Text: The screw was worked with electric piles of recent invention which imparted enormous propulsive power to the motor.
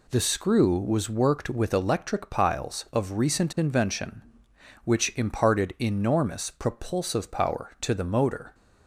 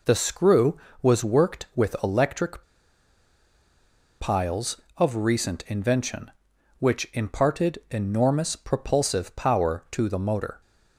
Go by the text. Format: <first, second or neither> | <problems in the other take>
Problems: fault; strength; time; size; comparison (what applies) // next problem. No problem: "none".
first | pauses between "electric" and "piles"; strong; at 2.6 s; 1.5 s long